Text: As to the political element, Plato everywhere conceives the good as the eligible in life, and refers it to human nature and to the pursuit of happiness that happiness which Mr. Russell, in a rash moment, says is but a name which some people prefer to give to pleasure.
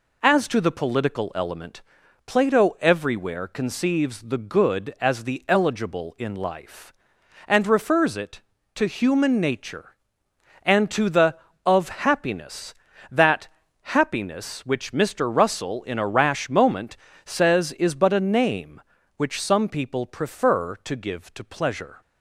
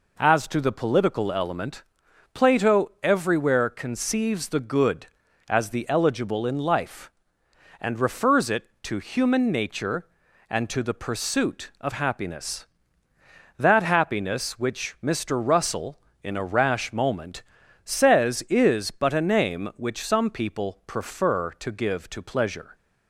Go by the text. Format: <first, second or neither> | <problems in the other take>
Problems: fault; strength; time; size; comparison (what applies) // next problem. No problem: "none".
second | skips "pursuit"; at 11.5 s // pauses between "that" and "happiness"; slight; at 13.4 s; 0.32 s long